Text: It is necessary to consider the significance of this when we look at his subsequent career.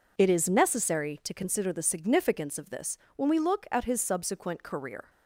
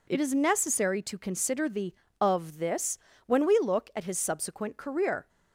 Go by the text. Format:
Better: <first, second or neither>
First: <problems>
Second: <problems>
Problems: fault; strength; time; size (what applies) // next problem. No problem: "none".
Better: first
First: pauses between "this" and "when"; slight; at 2.9 s; 0.20 s long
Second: skips "significance"; at 2.0 s // pauses between "this" and "when"; slight; at 2.9 s; 0.28 s long